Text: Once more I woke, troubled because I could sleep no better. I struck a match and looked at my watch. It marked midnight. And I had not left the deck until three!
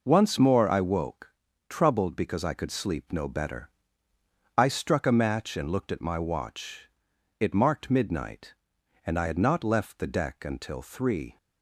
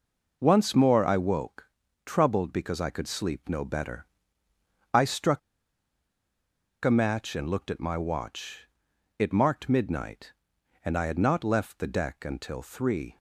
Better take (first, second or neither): first